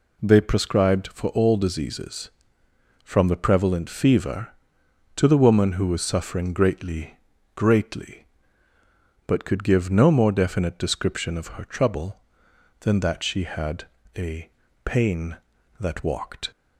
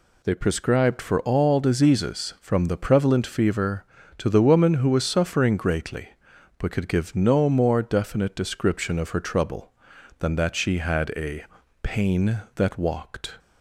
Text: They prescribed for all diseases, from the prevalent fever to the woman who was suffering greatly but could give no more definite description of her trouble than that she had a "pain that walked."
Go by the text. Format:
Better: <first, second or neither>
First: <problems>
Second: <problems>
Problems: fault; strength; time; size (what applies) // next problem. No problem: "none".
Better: second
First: says "greatly" twice; at 7.5 s // pauses between "had" and "a"; slight; at 13.8 s; 0.32 s long // pauses between "a" and "pain"; slight; at 14.4 s; 0.36 s long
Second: pauses between "a" and "pain"; at 11.4 s; 0.38 s long